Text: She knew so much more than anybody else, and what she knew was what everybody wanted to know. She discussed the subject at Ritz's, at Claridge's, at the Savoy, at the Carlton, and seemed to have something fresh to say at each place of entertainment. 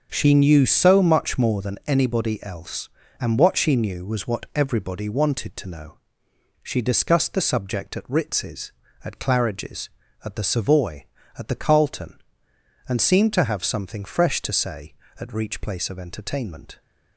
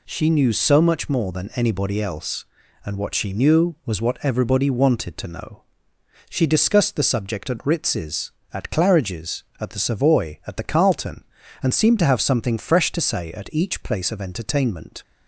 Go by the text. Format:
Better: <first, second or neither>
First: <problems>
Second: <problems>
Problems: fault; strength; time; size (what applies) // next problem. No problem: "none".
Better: second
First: starts louder than the rest; until 1.1 s; 6.5 dB // says "reach" for "each"; at 15.3 s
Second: none